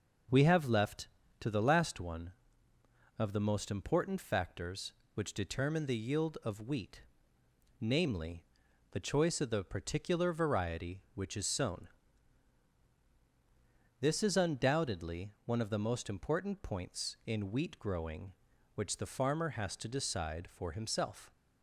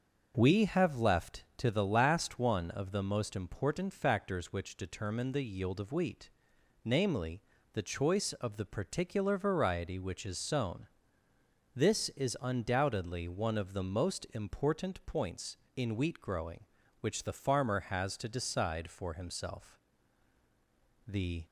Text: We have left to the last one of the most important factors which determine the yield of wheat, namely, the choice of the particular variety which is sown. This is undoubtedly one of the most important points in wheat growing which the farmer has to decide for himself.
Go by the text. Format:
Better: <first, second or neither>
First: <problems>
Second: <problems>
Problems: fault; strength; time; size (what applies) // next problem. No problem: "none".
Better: first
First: none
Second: starts louder than the rest; until 1.3 s; 6 dB // goes on to say "The"; slight; from 21.0 s on; 0.38 s long